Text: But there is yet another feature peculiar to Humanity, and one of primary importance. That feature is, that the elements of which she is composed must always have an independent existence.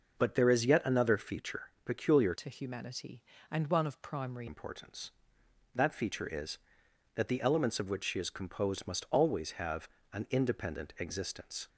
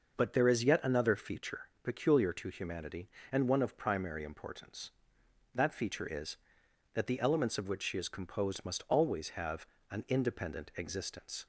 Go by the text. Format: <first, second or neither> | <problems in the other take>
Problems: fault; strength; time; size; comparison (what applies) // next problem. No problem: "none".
second | pauses between "feature" and "peculiar"; slight; at 1.6 s; 0.16 s long; slight in the second // changes voice from "to" to "primary"; from 2.3 to 4.4 s; 2.1 s long // pauses between "have" and "an"; slight; at 9.8 s; 0.24 s long; slight in the second